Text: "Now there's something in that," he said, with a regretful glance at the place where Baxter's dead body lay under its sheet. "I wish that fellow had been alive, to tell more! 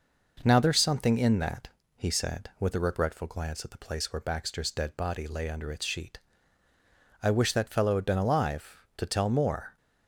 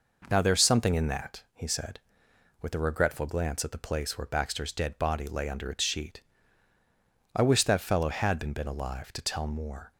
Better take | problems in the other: first | says "been" twice; at 8.5 s

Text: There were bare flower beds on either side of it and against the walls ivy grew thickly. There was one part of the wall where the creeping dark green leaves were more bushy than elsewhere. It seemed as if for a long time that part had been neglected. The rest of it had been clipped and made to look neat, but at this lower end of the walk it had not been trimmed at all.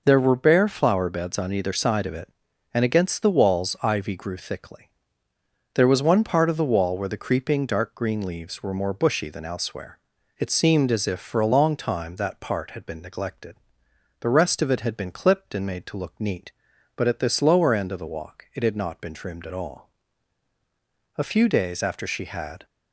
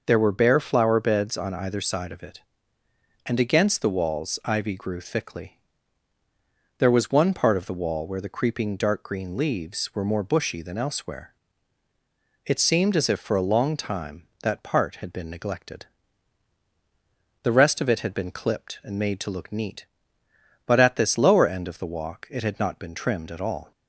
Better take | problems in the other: second | goes on to say "A few days after she had"; from 21.1 s on; 1.4 s long

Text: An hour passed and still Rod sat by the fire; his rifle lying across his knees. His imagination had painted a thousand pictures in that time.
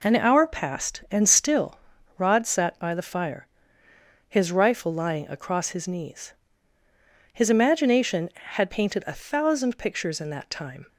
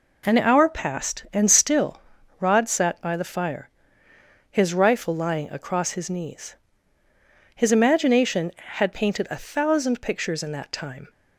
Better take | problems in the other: neither | pauses between "still" and "Rod"; the same in both

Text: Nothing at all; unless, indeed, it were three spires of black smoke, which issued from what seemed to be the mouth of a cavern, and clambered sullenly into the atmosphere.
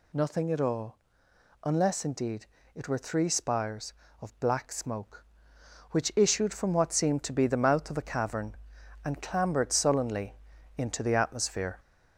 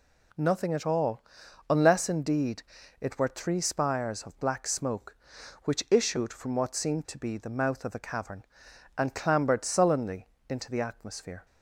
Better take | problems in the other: second | gets louder; slight; throughout; 3 dB // pauses between "sullenly" and "into"; at 10.3 s; 0.44 s long; slight in the second

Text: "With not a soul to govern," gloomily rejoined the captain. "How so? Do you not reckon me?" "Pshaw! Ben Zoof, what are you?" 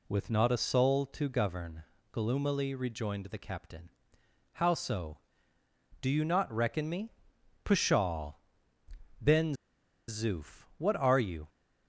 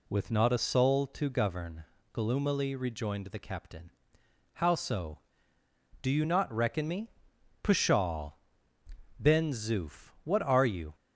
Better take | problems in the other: second | pauses between "Ben" and "Zoof"; noticeable; at 9.5 s; 0.55 s long

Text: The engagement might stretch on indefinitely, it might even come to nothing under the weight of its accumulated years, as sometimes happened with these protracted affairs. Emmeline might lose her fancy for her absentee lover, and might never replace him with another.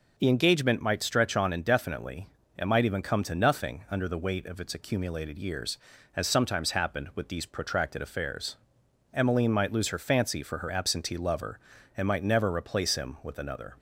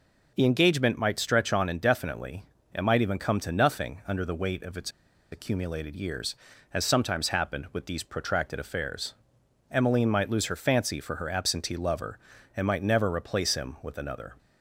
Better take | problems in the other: first | pauses between "its" and "accumulated"; at 4.8 s; 0.42 s long

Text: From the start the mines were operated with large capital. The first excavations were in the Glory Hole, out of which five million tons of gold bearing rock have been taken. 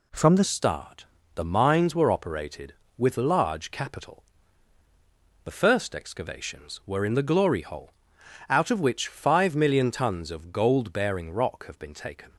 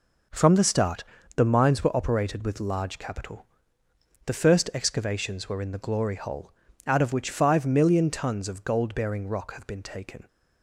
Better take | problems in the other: second | changes voice at "start"; from 0.4 s on; 11.9 s long // pauses between "start" and "the"; slight; at 1.0 s; 0.30 s long; slight in the second

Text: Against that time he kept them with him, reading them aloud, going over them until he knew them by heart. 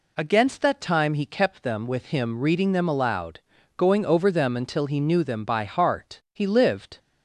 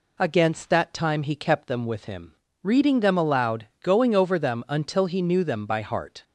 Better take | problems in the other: second | goes on to say "He lived"; noticeable; from 6.3 s on; 0.64 s long

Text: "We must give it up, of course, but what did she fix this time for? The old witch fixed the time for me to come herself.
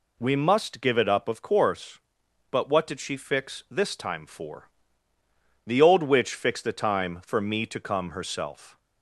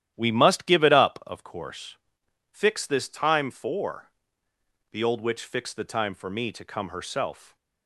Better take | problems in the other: first | starts louder than the rest; strong; until 1.1 s; 11.5 dB // skips "but what did she"; at 2.2 s

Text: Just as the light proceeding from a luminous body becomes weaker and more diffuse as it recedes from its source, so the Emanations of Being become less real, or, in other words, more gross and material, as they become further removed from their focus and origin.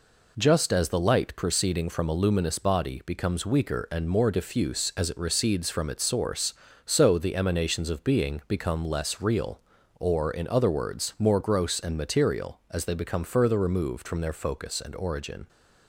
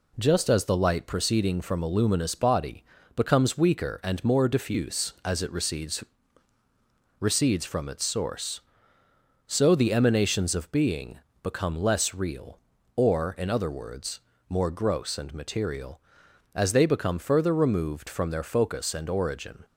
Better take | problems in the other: first | pauses between "body" and "becomes"; slight; at 2.8 s; 0.32 s long // says "recedes" twice; at 7.1 s // pauses between "Being" and "become"; slight; at 11.1 s; 0.22 s long

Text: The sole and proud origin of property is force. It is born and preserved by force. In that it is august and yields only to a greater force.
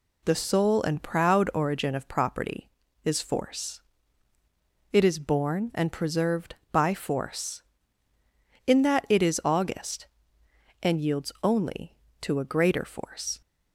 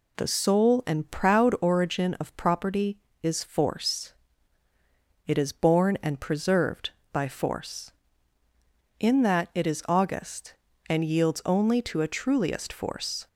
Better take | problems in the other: first | says "truliest" for "greater"; at 12.0 s

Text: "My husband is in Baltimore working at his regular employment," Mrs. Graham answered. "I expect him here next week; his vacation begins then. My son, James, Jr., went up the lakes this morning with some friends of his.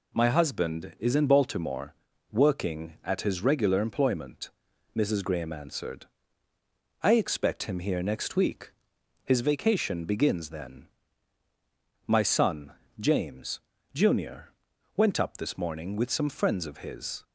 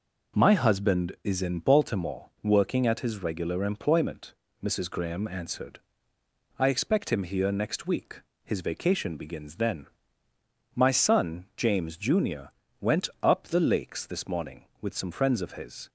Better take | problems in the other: second | pauses between "Baltimore" and "working"; slight; at 1.9 s; 0.36 s long // skips "the lakes"; at 15.3 s

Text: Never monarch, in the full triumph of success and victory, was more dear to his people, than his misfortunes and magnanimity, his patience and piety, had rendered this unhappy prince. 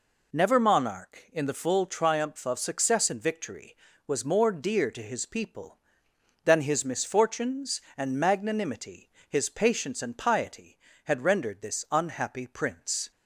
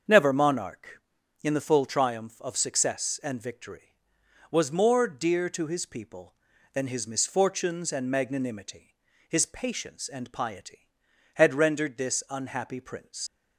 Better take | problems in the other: first | starts louder than the rest; until 1.5 s; 6.5 dB // leaves "prince" unfinished; at 13.2 s; 90 ms

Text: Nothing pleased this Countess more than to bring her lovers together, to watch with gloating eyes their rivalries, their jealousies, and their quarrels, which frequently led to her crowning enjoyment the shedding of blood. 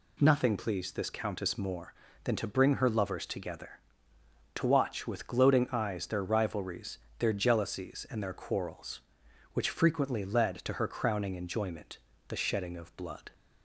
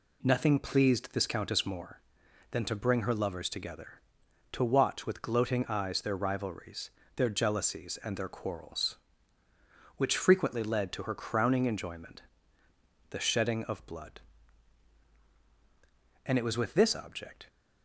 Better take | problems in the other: first | pauses between "enjoyment" and "the"; noticeable; at 12.2 s; 0.87 s long; slight in the first // goes on to say "And it was with this object"; noticeable; from 16.2 s on; 1.2 s long

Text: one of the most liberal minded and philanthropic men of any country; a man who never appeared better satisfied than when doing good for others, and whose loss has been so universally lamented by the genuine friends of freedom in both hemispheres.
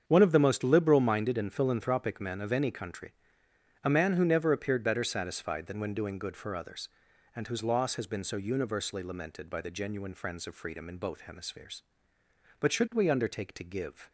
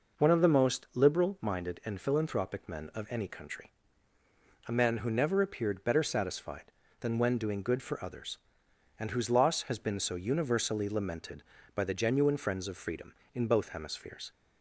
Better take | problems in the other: second | starts louder than the rest; strong; until 1.0 s; 7.5 dB // goes on to say "But should we undertake to give"; from 12.5 s on; 1.5 s long

